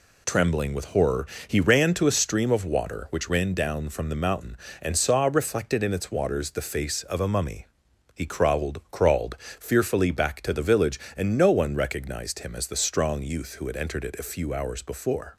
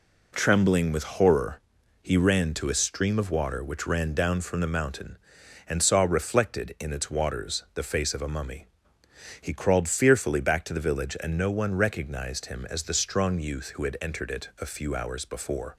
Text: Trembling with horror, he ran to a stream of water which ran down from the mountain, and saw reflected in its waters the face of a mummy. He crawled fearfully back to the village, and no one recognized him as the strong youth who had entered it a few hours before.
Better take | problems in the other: second | says "crawled" twice; at 8.9 s

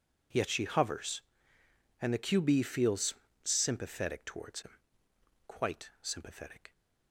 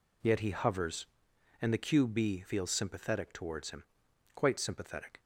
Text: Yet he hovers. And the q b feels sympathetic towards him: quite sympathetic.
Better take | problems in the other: second | says "she" for "he"; at 0.4 s // pauses between "feels" and "sympathetic"; slight; at 3.1 s; 0.30 s long

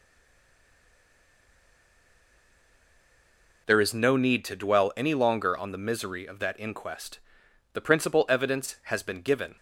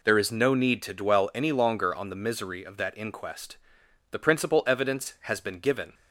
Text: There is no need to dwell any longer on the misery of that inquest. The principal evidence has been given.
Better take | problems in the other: second | stays silent before the first word; strong; until 3.6 s; 3.6 s long

